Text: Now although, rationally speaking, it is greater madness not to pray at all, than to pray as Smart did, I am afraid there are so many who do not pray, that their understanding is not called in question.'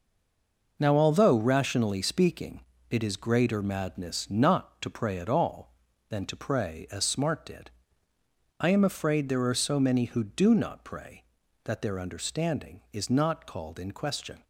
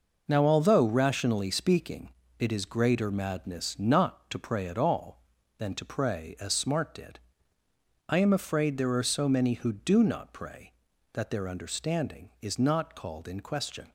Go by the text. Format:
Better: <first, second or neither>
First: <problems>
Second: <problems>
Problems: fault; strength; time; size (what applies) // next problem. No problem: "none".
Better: second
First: stays silent before the first word; slight; until 0.7 s; 0.7 s long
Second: none